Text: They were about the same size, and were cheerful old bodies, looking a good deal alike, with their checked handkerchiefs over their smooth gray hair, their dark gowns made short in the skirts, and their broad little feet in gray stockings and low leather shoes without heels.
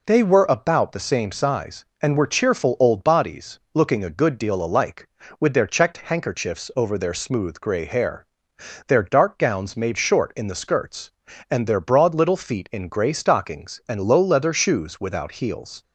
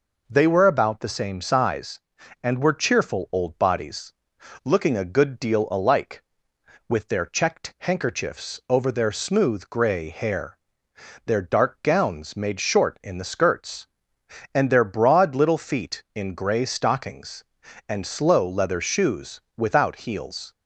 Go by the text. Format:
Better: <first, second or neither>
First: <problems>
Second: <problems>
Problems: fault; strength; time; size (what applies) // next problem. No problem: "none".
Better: first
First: none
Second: says "slow" for "low"; at 18.0 s // pauses between "shoes" and "without"; slight; at 19.4 s; 0.16 s long